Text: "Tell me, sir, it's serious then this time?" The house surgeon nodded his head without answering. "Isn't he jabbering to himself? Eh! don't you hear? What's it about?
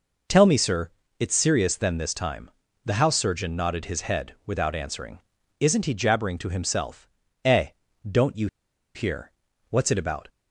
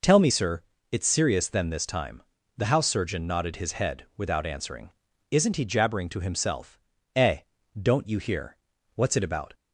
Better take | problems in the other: second | pauses between "you" and "hear"; noticeable; at 8.4 s; 0.48 s long

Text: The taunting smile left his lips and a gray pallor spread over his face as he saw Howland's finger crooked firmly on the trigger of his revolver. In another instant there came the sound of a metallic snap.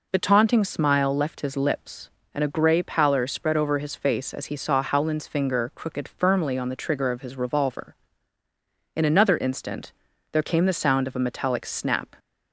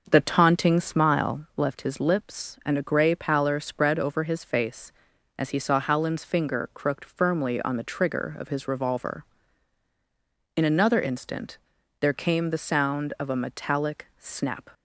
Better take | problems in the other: first | starts louder than the rest; noticeable; until 1.2 s; 6 dB // pauses between "instant" and "there"; at 11.5 s; 0.44 s long; also in the first

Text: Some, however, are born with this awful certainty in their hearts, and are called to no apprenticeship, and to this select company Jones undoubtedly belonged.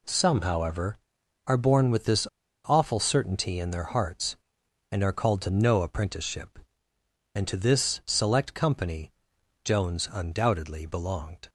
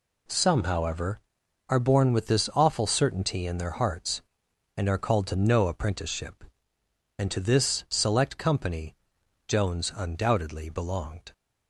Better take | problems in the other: second | pauses between "this" and "awful"; at 2.2 s; 0.39 s long // pauses between "company" and "Jones"; noticeable; at 9.1 s; 0.52 s long; noticeable in the second

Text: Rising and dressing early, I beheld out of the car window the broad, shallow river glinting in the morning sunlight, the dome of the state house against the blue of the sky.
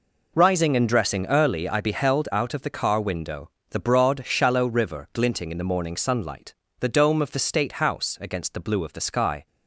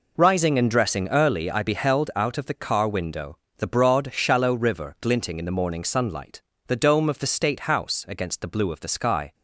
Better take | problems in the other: neither | pauses between "window" and "the"; slight; the same in both

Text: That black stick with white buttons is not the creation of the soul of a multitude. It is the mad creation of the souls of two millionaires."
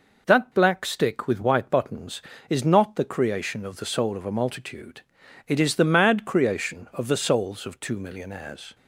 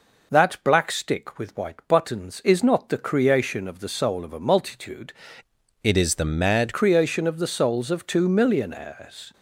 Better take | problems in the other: first | changes voice from "It" to "mad"; from 5.8 to 6.7 s; 0.9 s long

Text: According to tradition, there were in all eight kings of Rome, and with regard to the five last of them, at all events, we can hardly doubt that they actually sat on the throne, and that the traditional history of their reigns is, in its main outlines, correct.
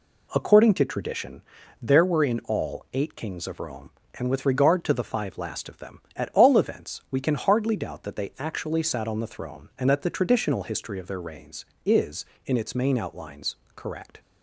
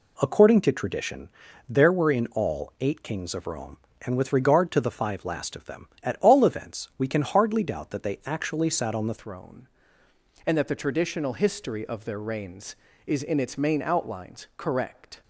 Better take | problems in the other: first | changes voice at "throne"; from 9.1 s on; 6.1 s long

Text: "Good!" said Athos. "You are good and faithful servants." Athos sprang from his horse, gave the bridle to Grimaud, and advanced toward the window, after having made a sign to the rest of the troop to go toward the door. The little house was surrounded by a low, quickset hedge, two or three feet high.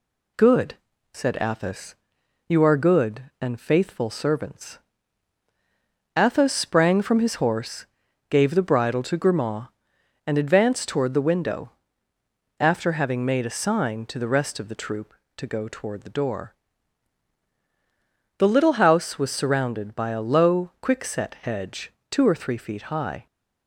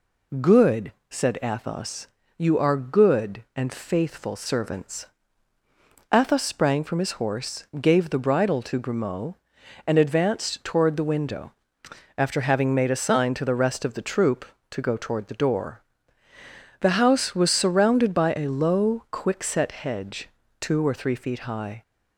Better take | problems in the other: first | skips "little"; at 16.8 s

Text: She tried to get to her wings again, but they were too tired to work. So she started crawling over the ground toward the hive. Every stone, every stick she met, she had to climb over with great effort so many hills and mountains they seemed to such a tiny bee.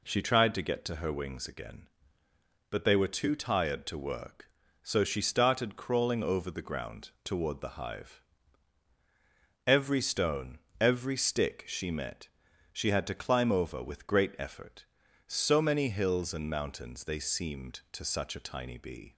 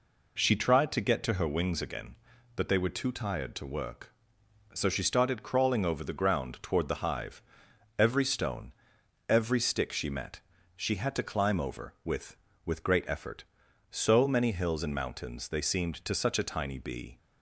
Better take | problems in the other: first | says "with" twice; at 12.6 s

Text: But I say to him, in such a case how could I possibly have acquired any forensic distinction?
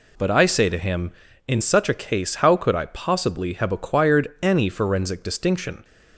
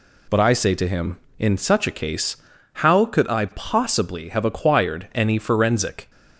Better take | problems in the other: first | pauses between "case" and "how"; at 2.3 s; 0.38 s long // stops before "distinction"; at 6.0 s

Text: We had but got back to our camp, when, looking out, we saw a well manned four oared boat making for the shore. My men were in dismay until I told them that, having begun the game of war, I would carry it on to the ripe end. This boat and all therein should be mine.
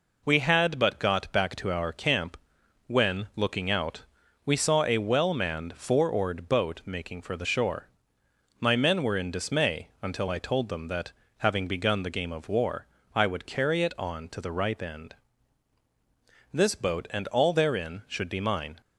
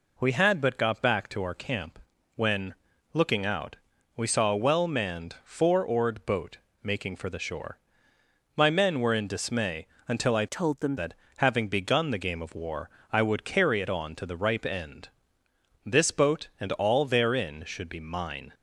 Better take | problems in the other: first | pauses between "boat" and "making"; slight; at 6.5 s; 0.26 s long // pauses between "dismay" and "until"; slight; at 9.8 s; 0.22 s long // changes voice from "told" to "them"; from 10.4 to 10.9 s; 0.5 s long

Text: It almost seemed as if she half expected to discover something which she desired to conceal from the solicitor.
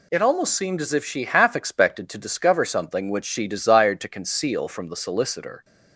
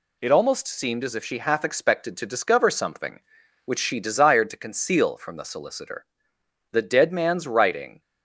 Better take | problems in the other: first | goes on to say "The dead man's writing"; noticeable; from 6.7 s on; 1.2 s long

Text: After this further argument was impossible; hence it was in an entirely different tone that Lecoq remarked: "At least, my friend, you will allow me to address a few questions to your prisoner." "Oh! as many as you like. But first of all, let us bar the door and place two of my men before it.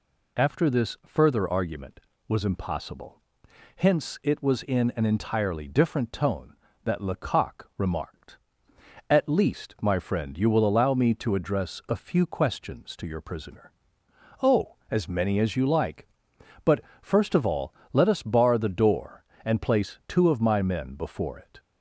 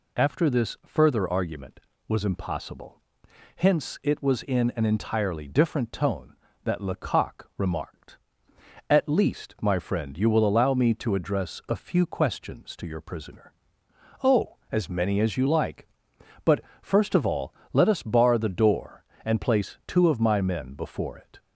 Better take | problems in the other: neither | pauses between "But" and "first"; slight; the same in both

